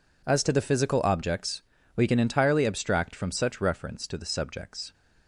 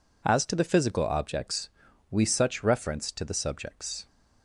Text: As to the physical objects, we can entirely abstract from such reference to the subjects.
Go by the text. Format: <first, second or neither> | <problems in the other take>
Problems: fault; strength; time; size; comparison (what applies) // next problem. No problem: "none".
first | skips "can entirely abstract from"; at 2.2 s